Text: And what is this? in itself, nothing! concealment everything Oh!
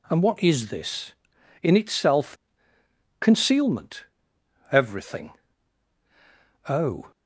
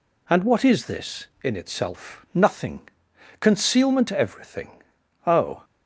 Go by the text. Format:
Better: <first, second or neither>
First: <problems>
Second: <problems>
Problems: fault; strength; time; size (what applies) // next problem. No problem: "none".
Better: second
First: skips "nothing"; at 2.7 s // pauses between "concealment" and "everything"; noticeable; at 4.0 s; 0.70 s long // pauses between "everything" and "Oh"; strong; at 5.3 s; 1.3 s long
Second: pauses between "everything" and "Oh"; at 4.8 s; 0.44 s long